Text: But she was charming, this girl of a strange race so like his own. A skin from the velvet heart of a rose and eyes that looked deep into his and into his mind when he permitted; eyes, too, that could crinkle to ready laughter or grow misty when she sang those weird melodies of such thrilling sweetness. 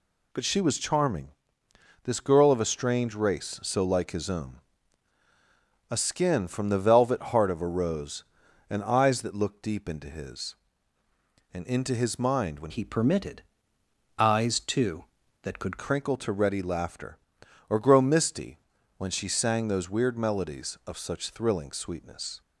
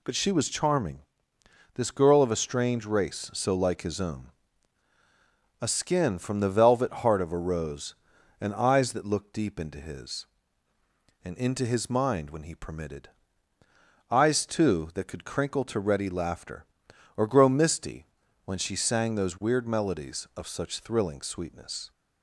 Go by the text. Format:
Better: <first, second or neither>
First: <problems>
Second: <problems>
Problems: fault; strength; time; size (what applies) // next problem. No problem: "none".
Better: second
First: changes voice from "he" to "could"; from 12.6 to 15.7 s; 3.1 s long // pauses between "misty" and "when"; at 18.5 s; 0.38 s long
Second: pauses between "misty" and "when"; at 18.0 s; 0.38 s long